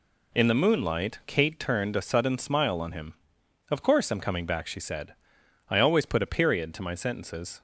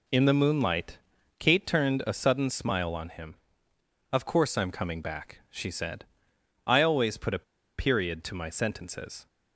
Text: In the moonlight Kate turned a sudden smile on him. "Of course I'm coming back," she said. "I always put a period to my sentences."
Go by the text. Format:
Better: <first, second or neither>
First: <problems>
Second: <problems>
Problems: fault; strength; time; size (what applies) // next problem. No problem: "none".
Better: first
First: none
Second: pauses between "moonlight" and "Kate"; at 0.9 s; 0.42 s long // pauses between "a" and "period"; slight; at 7.4 s; 0.36 s long